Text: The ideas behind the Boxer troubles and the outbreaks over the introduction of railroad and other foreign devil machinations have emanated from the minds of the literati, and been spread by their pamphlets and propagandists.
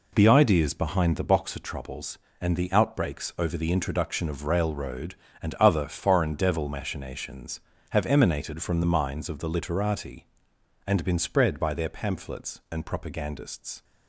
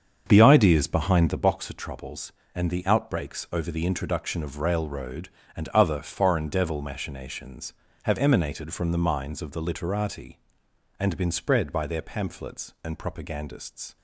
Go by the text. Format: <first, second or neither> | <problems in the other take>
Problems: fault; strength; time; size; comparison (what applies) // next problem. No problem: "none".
first | starts louder than the rest; until 1.5 s; 7 dB